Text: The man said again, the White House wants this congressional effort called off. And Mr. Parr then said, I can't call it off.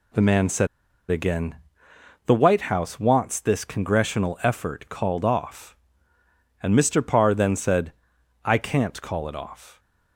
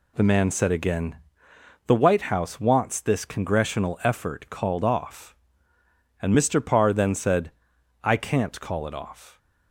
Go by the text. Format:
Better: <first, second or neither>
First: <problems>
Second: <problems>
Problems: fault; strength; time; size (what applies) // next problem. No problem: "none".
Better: second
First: pauses between "said" and "again"; at 0.6 s; 0.41 s long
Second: none